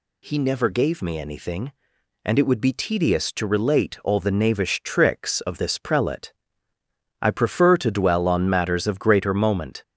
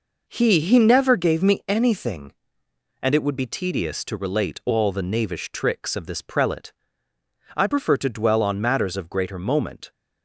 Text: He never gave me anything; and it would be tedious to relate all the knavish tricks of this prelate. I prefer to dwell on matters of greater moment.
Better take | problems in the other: first | says "He" twice; at 0.5 s

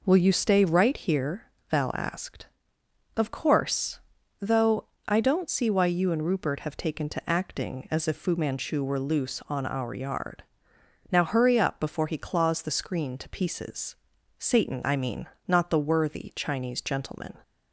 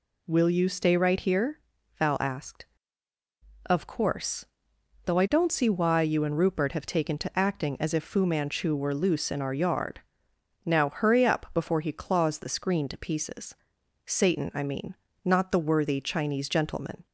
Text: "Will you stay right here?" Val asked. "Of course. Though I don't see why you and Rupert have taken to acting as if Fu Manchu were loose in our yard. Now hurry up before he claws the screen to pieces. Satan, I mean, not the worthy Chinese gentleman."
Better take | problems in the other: second | pauses between "Though" and "I"; slight; at 4.8 s; 0.20 s long // says "on" for "in"; at 9.4 s

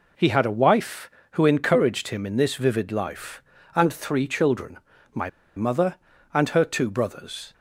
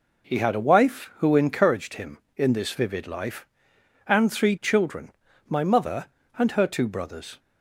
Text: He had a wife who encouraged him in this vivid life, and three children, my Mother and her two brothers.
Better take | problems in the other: second | pauses between "my" and "Mother"; slight; at 5.2 s; 0.28 s long

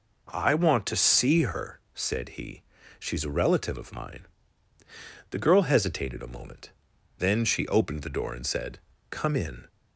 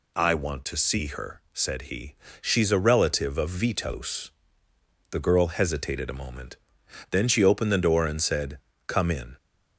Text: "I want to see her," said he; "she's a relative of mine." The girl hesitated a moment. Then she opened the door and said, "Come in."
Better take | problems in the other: first | says "vitos" for "mine"; at 3.4 s

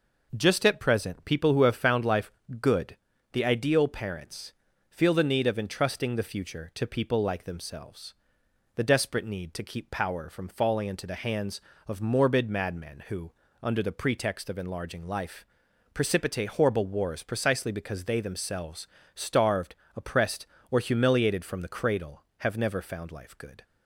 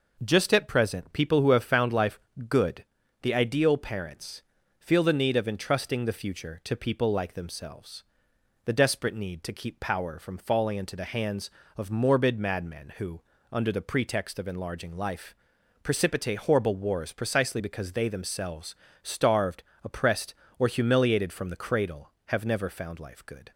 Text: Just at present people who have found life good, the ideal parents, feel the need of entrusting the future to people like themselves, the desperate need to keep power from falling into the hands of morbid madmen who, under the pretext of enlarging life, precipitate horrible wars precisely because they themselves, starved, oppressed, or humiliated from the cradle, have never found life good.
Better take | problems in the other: neither | pauses between "life" and "good"; slight; the same in both

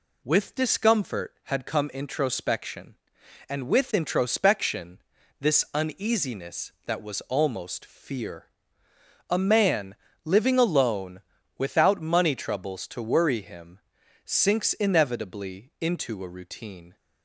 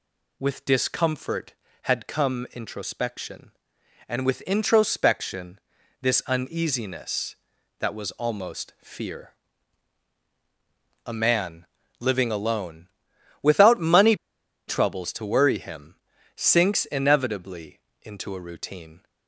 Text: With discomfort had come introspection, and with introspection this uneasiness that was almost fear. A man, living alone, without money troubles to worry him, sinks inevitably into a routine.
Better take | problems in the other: first | pauses between "introspection" and "this"; at 5.5 s; 0.42 s long; also in the first // pauses between "money" and "troubles"; noticeable; at 14.1 s; 0.52 s long // pauses between "inevitably" and "into"; slight; at 17.8 s; 0.22 s long

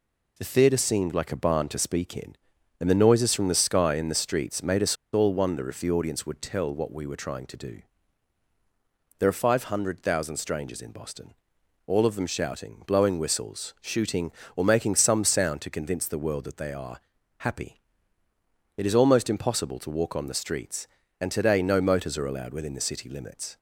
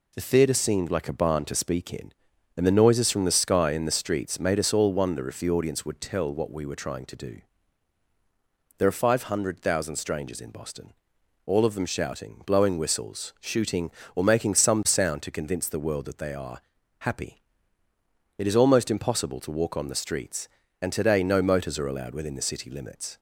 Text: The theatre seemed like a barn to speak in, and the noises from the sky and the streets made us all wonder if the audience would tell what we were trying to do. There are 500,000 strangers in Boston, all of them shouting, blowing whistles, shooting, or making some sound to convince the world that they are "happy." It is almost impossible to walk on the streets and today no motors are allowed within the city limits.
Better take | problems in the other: second | pauses between "us" and "all"; slight; at 4.9 s; 0.18 s long // pauses between "are" and "happy"; at 16.9 s; 0.38 s long; also in the second

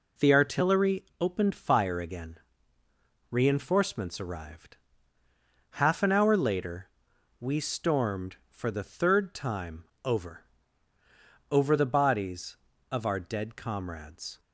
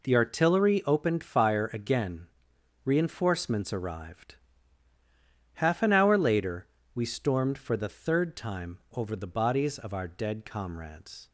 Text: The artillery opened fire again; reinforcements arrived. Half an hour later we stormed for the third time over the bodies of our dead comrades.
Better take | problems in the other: second | pauses between "artillery" and "opened"; slight; at 1.0 s; 0.18 s long // pauses between "later" and "we"; noticeable; at 6.8 s; 0.50 s long; slight in the second // pauses between "time" and "over"; slight; at 9.8 s; 0.20 s long // says "over" twice; at 11.5 s

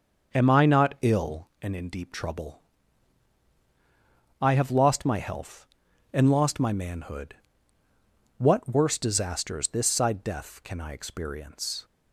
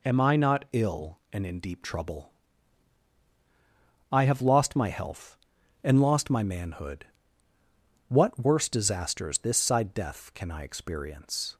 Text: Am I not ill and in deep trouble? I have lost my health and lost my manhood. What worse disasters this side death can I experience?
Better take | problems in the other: second | starts louder than the rest; until 1.5 s; 6 dB

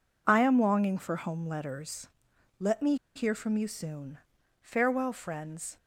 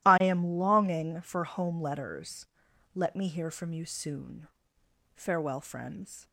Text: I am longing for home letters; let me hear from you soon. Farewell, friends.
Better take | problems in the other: second | pauses between "me" and "hear"; slight; at 2.9 s; 0.20 s long

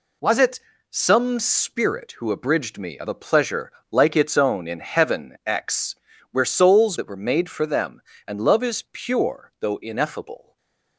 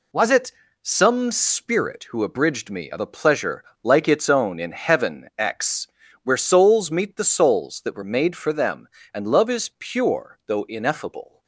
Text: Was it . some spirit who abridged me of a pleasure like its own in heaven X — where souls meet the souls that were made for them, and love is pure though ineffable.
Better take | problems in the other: second | pauses between "pleasure" and "like"; slight; at 3.7 s; 0.18 s long; slight in the second // skips "meet the souls"; at 6.9 s // stays silent after the last word; slight; from 10.4 s on; 0.5 s long

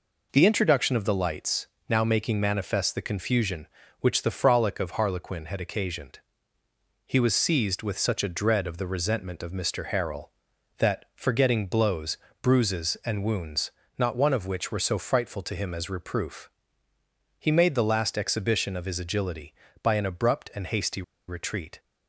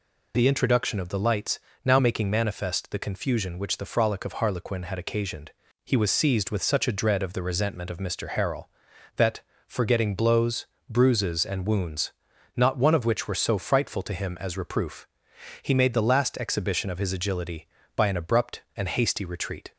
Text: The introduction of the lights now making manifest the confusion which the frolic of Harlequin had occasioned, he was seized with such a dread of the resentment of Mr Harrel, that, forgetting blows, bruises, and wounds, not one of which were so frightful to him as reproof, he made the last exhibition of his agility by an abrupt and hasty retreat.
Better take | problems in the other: second | pauses between "lights" and "now"; slight; at 1.6 s; 0.22 s long; slight in the second // pauses between "hasty" and "retreat"; slight; at 21.0 s; 0.26 s long

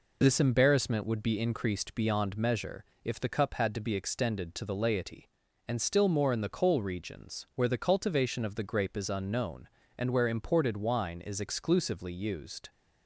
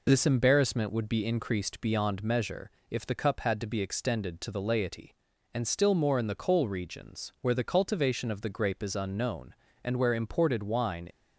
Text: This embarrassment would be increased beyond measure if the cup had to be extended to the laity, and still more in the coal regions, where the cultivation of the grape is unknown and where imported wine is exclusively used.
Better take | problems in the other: first | pauses between "measure" and "if"; slight; at 2.7 s; 0.18 s long; slight in the first // stops before "is exclusively used"; at 11.1 s

